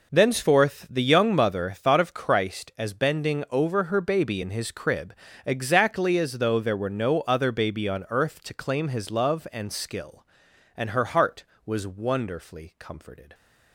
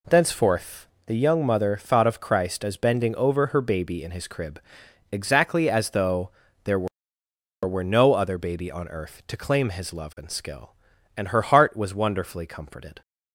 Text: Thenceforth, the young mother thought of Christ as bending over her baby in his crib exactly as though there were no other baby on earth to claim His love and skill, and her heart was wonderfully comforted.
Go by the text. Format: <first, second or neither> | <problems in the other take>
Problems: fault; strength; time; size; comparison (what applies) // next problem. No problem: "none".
first | pauses between "crib" and "exactly"; noticeable; at 4.5 s; 0.52 s long; slight in the first // pauses between "though" and "there"; slight; at 6.2 s; 0.34 s long // says "were" twice; at 7.6 s